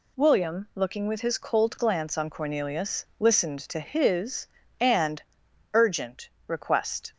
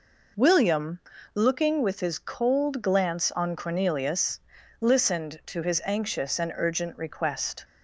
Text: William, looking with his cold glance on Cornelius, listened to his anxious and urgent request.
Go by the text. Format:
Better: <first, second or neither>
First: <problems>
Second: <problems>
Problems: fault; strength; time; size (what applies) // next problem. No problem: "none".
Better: second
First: skips "anxious"; at 4.6 s // pauses between "and" and "urgent"; noticeable; at 5.2 s; 0.50 s long // pauses between "urgent" and "request"; slight; at 6.2 s; 0.20 s long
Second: none